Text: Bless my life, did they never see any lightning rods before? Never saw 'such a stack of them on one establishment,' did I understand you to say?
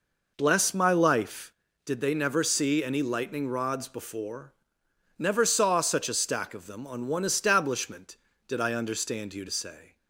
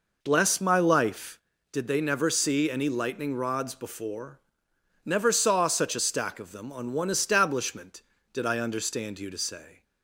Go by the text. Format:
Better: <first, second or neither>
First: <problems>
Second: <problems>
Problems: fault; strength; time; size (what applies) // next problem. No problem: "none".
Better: neither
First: none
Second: none